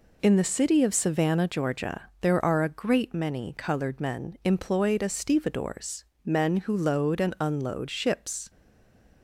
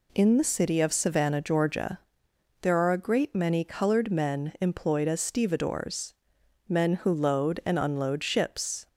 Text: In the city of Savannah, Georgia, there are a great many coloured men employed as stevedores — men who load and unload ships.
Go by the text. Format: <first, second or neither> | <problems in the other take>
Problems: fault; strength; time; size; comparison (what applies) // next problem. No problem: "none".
second | stays silent after the last word; slight; from 8.4 s on; 0.8 s long